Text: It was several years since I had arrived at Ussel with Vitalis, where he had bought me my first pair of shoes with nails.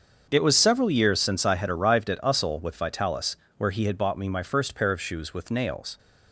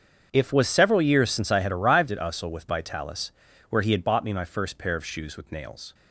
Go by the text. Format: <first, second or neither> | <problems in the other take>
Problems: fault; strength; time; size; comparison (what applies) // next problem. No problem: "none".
first | starts louder than the rest; strong; until 1.3 s; 7 dB; also in the first // says "If" for "It"; at 0.3 s